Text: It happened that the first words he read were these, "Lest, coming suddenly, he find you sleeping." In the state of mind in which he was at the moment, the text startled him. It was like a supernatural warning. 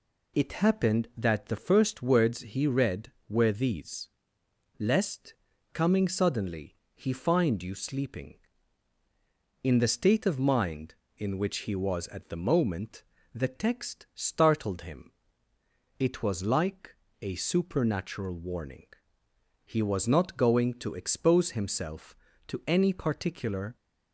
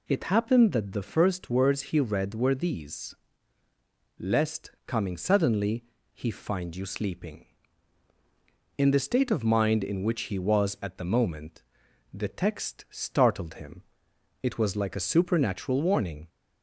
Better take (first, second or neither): second